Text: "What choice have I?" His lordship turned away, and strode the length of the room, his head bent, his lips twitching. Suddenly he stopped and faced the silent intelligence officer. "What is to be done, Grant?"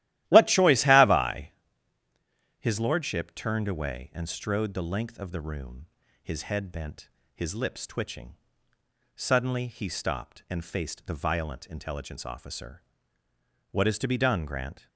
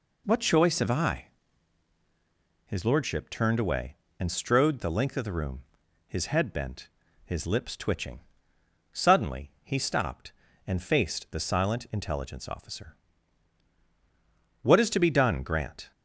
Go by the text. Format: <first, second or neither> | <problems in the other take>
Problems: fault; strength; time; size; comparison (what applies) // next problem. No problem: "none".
second | starts louder than the rest; strong; until 1.3 s; 14.5 dB // says "violent" for "silent"; at 11.1 s